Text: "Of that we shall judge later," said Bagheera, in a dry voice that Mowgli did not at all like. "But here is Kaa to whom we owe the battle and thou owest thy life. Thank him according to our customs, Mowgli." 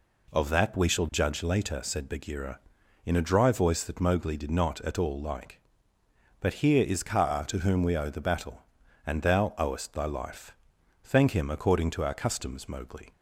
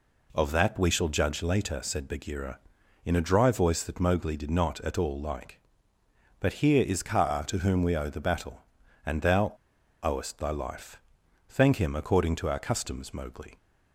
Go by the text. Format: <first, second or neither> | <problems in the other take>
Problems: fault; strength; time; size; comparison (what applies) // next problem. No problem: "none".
first | pauses between "thou" and "owest"; noticeable; at 9.5 s; 0.51 s long